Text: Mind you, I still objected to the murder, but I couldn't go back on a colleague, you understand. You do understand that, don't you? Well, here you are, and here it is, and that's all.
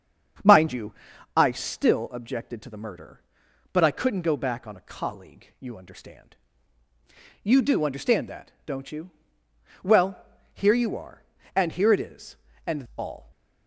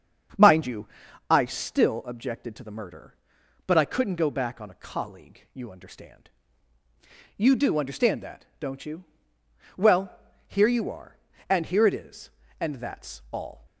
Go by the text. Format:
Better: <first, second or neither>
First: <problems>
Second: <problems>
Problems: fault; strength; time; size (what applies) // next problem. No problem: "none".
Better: second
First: starts louder than the rest; strong; until 1.8 s; 7 dB // skips "that's"; at 12.8 s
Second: starts louder than the rest; strong; until 1.7 s; 7 dB